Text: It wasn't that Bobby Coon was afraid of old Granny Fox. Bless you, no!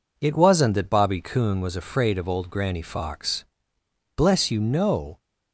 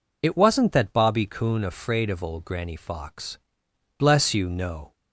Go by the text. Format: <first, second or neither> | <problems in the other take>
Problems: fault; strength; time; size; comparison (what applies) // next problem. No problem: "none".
first | skips "was"; at 1.6 s